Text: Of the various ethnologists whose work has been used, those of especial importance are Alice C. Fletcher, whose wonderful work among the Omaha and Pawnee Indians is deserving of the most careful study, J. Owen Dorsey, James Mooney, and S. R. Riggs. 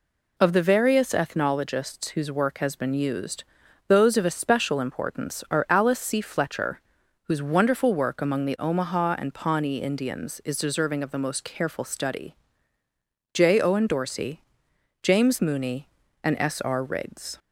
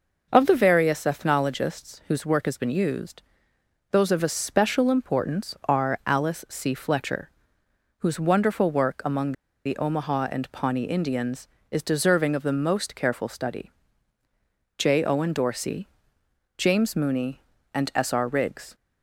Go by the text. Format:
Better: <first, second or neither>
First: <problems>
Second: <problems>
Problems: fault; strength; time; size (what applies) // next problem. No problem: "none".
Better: first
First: none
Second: pauses between "among" and "the"; slight; at 9.3 s; 0.33 s long